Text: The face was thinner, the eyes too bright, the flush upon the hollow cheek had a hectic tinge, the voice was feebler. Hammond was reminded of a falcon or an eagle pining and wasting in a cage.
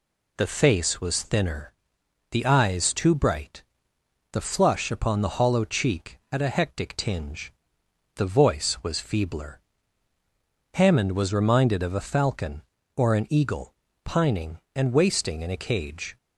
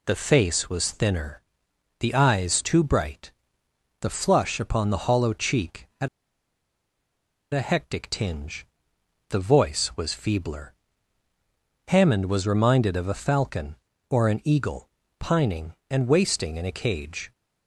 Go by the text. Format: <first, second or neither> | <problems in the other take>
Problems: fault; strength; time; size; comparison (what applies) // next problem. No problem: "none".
first | pauses between "had" and "a"; strong; at 6.0 s; 1.4 s long // pauses between "eagle" and "pining"; slight; at 14.8 s; 0.30 s long; slight in the first